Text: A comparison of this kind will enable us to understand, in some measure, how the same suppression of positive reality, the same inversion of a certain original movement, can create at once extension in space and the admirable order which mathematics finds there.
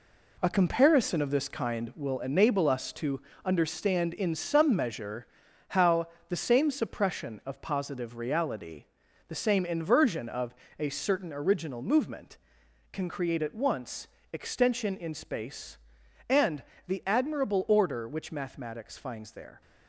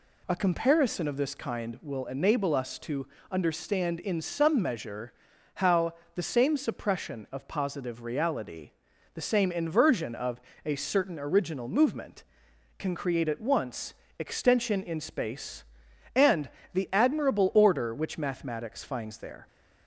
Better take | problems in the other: second | gets quieter; strong; throughout; 7.5 dB // pauses between "to" and "understand"; slight; at 3.2 s; 0.24 s long; slight in the second // pauses between "how" and "the"; slight; at 6.0 s; 0.22 s long; slight in the second // pauses between "of" and "a"; slight; at 10.5 s; 0.24 s long; slight in the second // pauses between "once" and "extension"; slight; at 14.0 s; 0.24 s long; slight in the second // pauses between "and" and "the"; slight; at 16.6 s; 0.24 s long; slight in the second

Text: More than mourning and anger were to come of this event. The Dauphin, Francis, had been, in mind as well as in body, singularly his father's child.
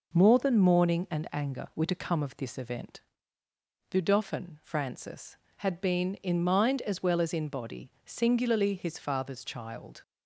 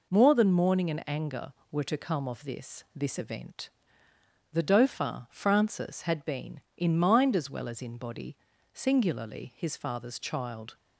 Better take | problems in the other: first | says "this" twice; at 2.9 s

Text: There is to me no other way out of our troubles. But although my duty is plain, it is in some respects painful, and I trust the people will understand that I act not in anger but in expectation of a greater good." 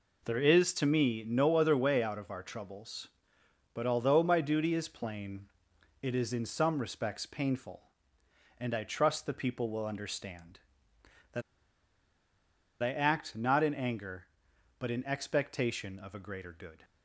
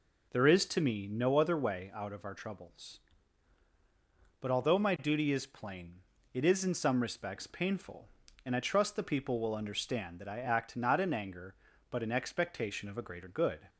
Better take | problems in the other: second | pauses between "that" and "I"; strong; at 11.4 s; 1.4 s long

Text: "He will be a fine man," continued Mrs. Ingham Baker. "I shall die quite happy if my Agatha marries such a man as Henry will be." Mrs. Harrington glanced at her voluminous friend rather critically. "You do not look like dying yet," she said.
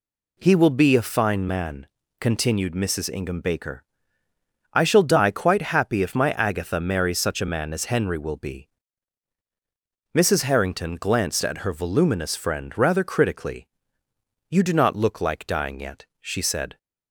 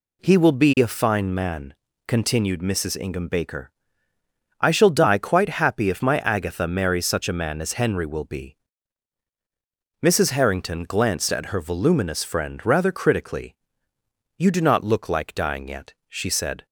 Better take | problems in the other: neither | none

